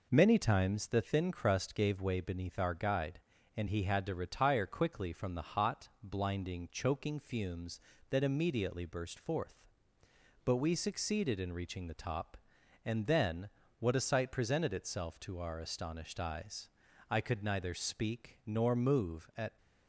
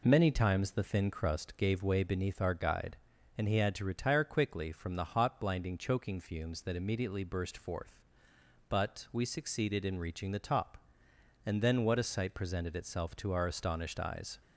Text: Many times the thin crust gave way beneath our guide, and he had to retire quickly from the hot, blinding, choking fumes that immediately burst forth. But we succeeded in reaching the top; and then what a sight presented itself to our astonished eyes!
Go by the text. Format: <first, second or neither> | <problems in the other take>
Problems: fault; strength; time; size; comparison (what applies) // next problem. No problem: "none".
second | pauses between "then" and "what"; slight; at 13.4 s; 0.32 s long // goes on to say "I could neither speak nor move at"; strong; from 17.1 s on; 2.4 s long